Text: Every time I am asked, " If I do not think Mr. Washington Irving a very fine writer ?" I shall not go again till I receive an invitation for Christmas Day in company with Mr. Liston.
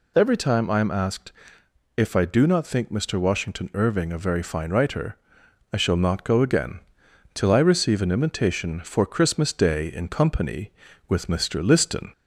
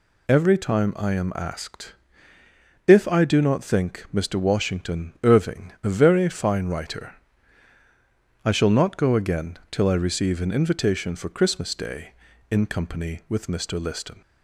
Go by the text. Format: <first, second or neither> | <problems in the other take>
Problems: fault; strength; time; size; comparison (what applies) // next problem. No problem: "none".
second | gets louder; throughout; 4 dB // pauses between "again" and "till"; noticeable; at 6.7 s; 0.56 s long